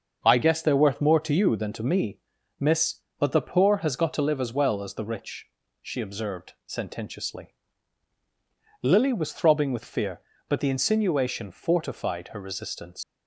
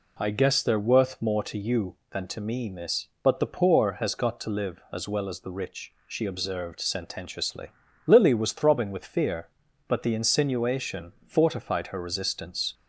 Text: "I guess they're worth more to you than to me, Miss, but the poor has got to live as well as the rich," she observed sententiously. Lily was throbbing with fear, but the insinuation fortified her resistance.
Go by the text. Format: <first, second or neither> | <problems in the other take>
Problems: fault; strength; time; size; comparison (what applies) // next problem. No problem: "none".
second | starts louder than the rest; until 1.2 s; 6.5 dB // leaves "resistance" unfinished; at 13.0 s; 105 ms